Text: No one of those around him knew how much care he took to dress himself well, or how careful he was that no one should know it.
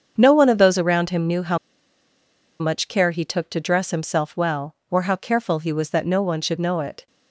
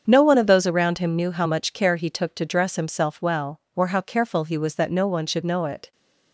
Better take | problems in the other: second | starts louder than the rest; strong; until 1.1 s; 7.5 dB; strong in the second // pauses between "how" and "much"; at 1.5 s; 1.0 s long

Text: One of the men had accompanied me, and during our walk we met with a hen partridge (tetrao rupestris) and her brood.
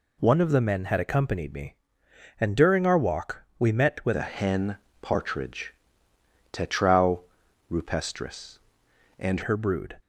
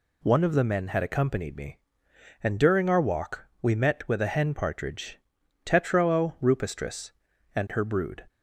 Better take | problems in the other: second | changes voice from "a" to "and"; from 4.1 to 9.4 s; 5.3 s long // pauses between "hen" and "partridge"; slight; at 4.7 s; 0.22 s long // pauses between "tetrao" and "rupestris"; noticeable; at 7.1 s; 0.50 s long

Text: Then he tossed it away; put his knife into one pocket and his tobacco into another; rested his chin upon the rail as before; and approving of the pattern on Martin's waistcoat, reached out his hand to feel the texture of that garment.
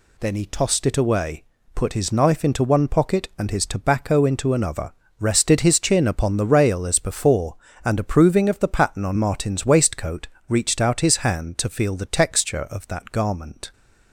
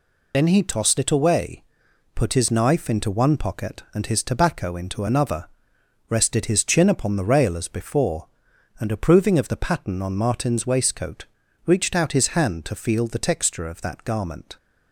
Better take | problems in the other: first | loses the start of "Then"; at 0.3 s; 45 ms

